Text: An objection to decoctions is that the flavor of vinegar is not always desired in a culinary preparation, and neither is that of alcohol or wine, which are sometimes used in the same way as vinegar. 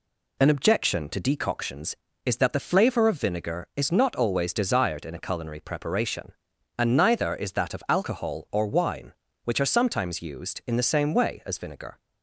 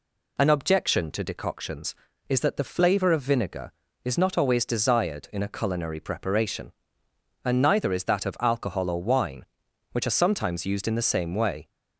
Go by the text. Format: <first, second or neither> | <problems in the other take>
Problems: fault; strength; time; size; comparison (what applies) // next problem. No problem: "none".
first | stops before "as vinegar"; at 11.6 s